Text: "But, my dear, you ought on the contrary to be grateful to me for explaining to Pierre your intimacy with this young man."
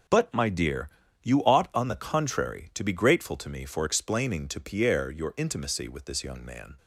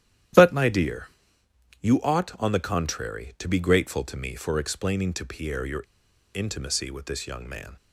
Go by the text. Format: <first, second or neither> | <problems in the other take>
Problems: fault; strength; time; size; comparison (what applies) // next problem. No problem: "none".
first | starts louder than the rest; strong; until 2.0 s; 11.5 dB // pauses between "your" and "intimacy"; noticeable; at 5.8 s; 0.50 s long